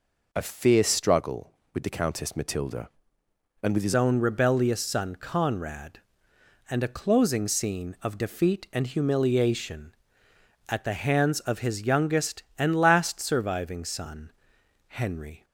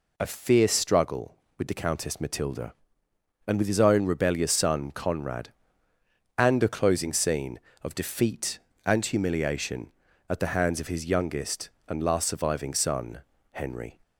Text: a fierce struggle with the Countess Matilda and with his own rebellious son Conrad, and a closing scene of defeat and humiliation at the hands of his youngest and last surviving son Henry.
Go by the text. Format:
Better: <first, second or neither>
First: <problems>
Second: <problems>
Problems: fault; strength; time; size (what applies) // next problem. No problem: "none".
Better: second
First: changes voice at "own"; from 3.9 s on; 11.5 s long // pauses between "son" and "Henry"; noticeable; at 14.3 s; 0.56 s long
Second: pauses between "son" and "Henry"; slight; at 13.2 s; 0.32 s long